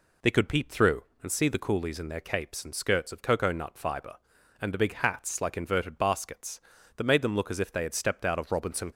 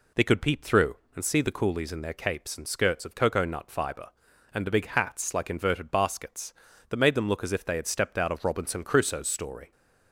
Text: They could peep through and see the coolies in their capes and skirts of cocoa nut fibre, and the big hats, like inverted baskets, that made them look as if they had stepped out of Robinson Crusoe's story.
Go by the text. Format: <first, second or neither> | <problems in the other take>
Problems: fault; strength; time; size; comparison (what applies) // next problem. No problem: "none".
second | stops before "Crusoe's story"; at 8.9 s